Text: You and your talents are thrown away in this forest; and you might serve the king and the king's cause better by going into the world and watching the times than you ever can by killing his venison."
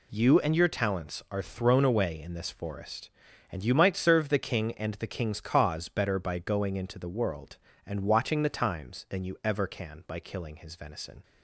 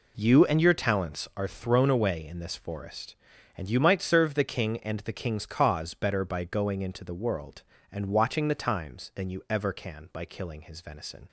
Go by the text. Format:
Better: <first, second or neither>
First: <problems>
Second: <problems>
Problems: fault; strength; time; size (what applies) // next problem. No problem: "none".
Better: first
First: none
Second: starts louder than the rest; slight; until 1.5 s; 3.5 dB